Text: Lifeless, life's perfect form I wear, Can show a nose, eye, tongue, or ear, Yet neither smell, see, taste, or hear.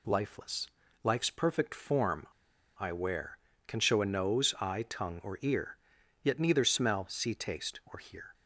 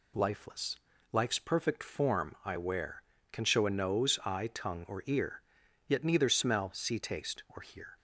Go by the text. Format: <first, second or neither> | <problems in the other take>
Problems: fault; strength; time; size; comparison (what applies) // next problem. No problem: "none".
second | pauses between "form" and "I"; noticeable; at 2.2 s; 0.51 s long